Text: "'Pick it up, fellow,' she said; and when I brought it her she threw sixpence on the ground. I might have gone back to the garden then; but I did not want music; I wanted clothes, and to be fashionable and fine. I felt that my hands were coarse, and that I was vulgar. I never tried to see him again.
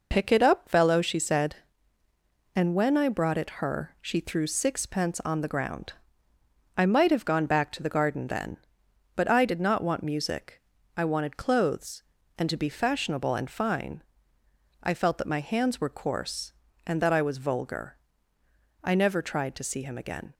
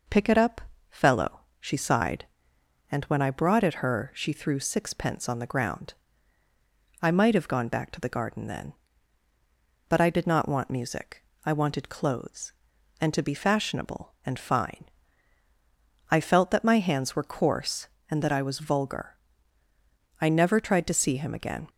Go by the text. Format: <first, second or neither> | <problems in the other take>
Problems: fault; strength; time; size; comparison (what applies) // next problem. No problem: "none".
first | says "sighed" for "said"; at 1.7 s